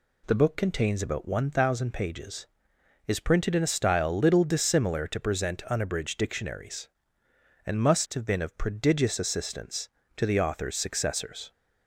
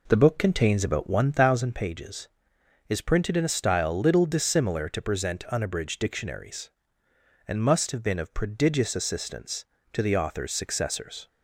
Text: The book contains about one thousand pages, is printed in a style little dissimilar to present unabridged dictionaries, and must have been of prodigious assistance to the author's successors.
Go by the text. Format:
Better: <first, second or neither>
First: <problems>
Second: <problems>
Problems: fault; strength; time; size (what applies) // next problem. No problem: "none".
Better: first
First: none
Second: starts louder than the rest; until 1.7 s; 3.5 dB